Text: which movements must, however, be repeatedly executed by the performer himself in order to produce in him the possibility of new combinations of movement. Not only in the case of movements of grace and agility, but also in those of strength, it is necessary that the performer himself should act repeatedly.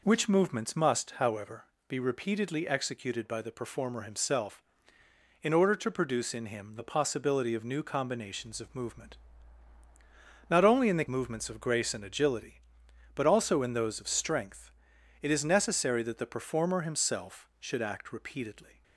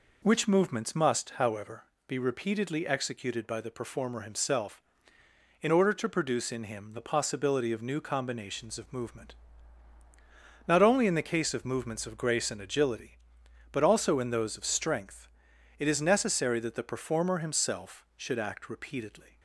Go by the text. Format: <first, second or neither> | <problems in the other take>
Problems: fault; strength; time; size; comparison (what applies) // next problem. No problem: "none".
second | skips "case of"; at 11.0 s